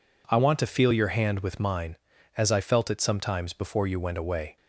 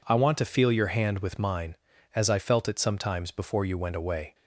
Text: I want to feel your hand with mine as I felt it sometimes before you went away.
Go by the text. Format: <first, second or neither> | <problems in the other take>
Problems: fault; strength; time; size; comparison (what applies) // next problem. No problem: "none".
neither | none